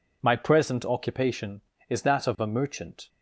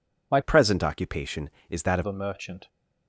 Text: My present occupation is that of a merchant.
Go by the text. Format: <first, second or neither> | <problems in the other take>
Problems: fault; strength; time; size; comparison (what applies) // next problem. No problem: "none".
first | changes voice from "present" to "of"; from 0.4 to 2.0 s; 1.6 s long